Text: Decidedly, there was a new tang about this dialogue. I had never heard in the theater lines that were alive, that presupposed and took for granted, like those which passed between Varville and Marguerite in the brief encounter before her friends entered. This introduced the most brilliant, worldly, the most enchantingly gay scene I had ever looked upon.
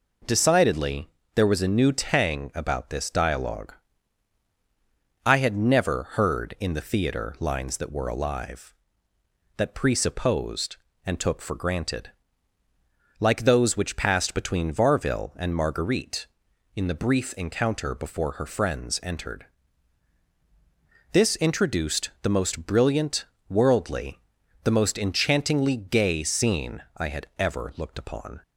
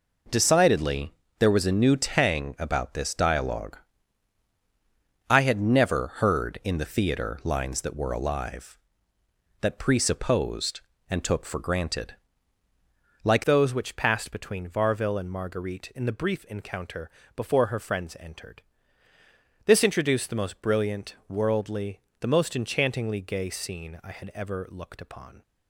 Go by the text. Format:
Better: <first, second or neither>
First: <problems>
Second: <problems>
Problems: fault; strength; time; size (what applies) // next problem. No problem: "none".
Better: first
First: none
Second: changes voice at "those"; from 13.4 s on; 12.0 s long // pauses between "encounter" and "before"; slight; at 17.0 s; 0.26 s long